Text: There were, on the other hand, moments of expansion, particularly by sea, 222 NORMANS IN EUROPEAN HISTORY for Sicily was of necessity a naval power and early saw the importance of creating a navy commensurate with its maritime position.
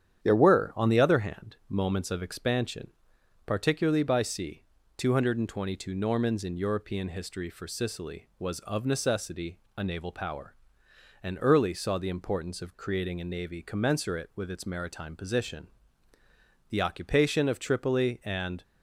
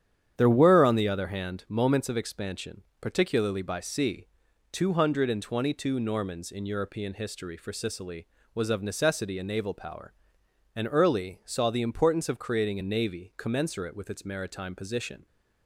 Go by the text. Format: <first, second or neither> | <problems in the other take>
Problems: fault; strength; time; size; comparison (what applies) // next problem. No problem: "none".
second | starts louder than the rest; strong; until 1.2 s; 9.5 dB; strong in the second // pauses between "necessity" and "a"; slight; at 9.5 s; 0.18 s long // goes on to say "The occupation of Tripoli and"; strong; from 16.7 s on; 1.9 s long